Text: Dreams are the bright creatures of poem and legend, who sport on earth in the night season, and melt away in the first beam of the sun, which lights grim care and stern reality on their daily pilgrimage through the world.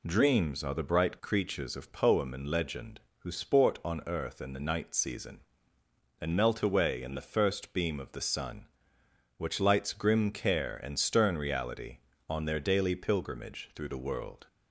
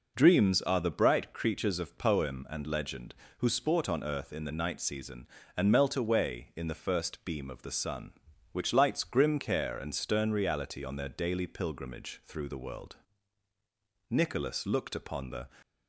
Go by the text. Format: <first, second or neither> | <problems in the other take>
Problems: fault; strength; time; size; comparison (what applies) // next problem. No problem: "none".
first | goes on to say "Nicholas looked upon the"; from 14.1 s on; 1.3 s long